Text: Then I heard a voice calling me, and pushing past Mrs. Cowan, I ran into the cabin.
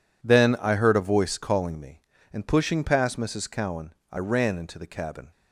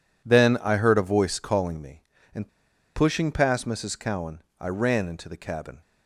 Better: first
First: none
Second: pauses between "and" and "pushing"; noticeable; at 2.4 s; 0.47 s long

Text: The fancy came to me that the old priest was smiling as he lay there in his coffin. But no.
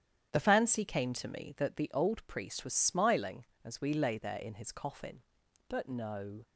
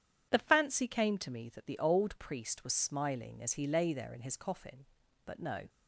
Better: second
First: starts louder than the rest; strong; until 1.3 s; 9.5 dB // says "we" for "he"; at 3.7 s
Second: none

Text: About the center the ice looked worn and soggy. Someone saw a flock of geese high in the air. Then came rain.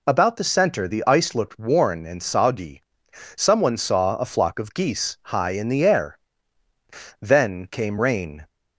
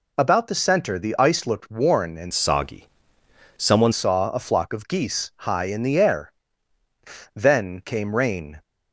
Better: first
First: none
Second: changes voice from "soggy" to "Someone"; from 2.3 to 3.9 s; 1.6 s long

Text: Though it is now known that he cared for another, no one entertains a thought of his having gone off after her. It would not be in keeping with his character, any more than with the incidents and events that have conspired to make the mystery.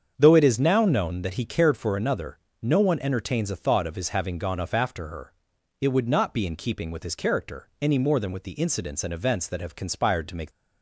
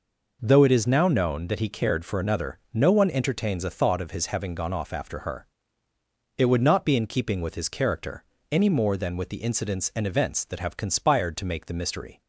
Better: second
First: starts louder than the rest; strong; until 1.1 s; 7.5 dB // stops before "the mystery"; at 10.5 s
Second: none

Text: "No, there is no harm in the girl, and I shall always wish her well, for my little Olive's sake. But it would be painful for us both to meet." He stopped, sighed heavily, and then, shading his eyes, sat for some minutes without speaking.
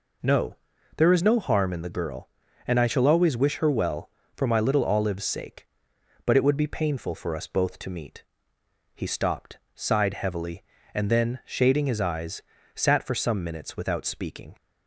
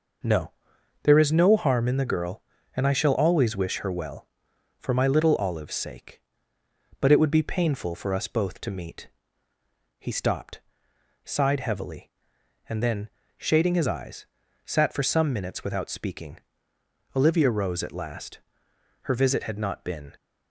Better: first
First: none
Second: goes on to say "Olivia rose at last Her visit had not been"; strong; from 17.1 s on; 3.0 s long

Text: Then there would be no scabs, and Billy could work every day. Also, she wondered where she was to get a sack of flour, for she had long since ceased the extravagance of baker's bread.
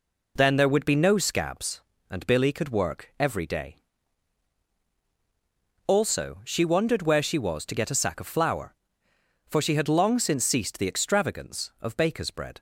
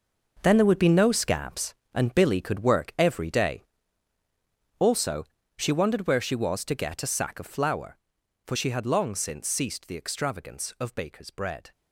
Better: first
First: none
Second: gets quieter; strong; throughout; 12.5 dB

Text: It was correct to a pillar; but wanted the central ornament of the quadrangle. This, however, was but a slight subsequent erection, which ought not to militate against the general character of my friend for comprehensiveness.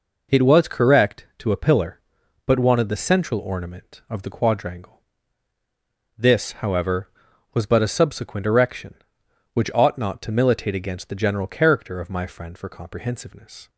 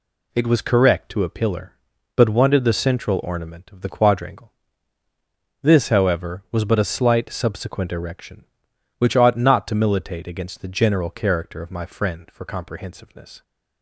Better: second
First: skips "slight"; at 7.8 s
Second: none

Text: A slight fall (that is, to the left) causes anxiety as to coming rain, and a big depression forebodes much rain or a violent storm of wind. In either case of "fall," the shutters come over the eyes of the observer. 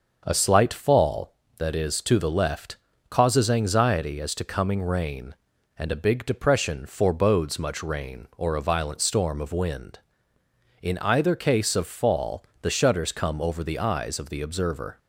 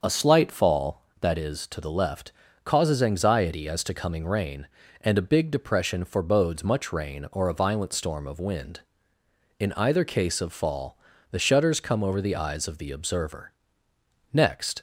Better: first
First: starts louder than the rest; noticeable; until 1.2 s; 6 dB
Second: starts louder than the rest; until 1.0 s; 6.5 dB // goes on to say "Next"; slight; from 14.3 s on; 0.48 s long

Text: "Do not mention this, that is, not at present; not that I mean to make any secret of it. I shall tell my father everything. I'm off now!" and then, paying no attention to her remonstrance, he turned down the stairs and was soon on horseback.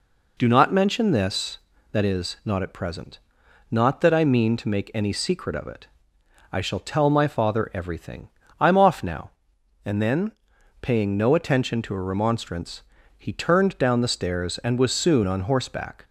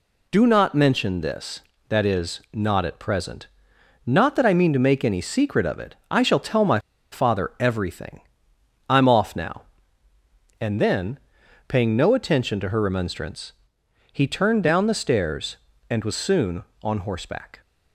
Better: first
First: none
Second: pauses between "my" and "father"; slight; at 6.7 s; 0.32 s long

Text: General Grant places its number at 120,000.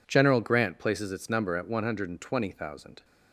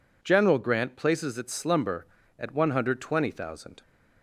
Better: first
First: none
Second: says "slumber" for "number"; at 1.5 s

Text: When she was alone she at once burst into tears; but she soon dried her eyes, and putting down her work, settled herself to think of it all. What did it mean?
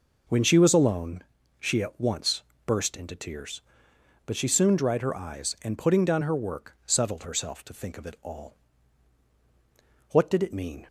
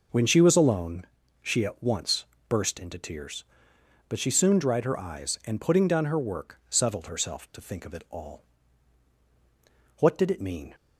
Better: neither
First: pauses between "alone" and "she"; slight; at 1.2 s; 0.36 s long // pauses between "once" and "burst"; slight; at 2.4 s; 0.24 s long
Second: pauses between "alone" and "she"; slight; at 1.0 s; 0.36 s long // pauses between "once" and "burst"; slight; at 2.2 s; 0.24 s long

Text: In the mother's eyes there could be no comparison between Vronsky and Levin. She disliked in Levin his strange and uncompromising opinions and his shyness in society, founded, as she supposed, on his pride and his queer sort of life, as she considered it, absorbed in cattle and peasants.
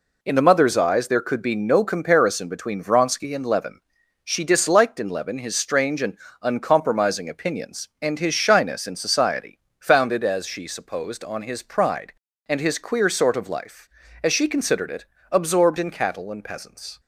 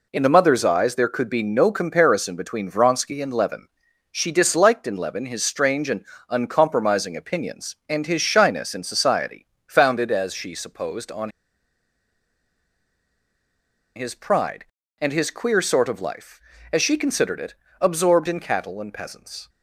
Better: first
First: pauses between "and" and "uncompromising"; slight; at 6.1 s; 0.28 s long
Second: pauses between "and" and "uncompromising"; slight; at 6.0 s; 0.28 s long // pauses between "on" and "his"; strong; at 11.2 s; 2.6 s long

